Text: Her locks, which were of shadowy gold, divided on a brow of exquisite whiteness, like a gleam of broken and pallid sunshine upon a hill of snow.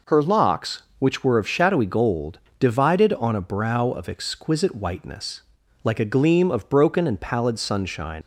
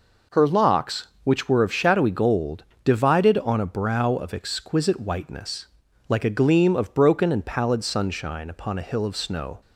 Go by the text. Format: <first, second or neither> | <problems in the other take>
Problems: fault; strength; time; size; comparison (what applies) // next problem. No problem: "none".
second | stops before "upon a hill of snow"; at 8.2 s